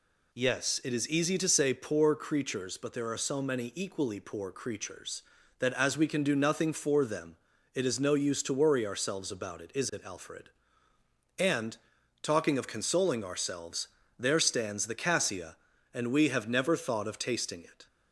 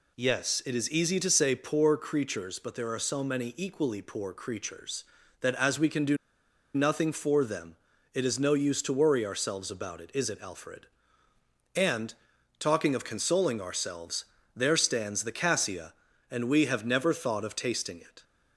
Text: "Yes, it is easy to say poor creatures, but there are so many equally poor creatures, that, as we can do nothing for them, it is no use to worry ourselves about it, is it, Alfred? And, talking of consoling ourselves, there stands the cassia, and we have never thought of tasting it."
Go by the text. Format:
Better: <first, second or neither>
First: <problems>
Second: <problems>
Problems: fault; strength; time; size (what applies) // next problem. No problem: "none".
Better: first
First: none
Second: pauses between "do" and "nothing"; noticeable; at 6.1 s; 0.59 s long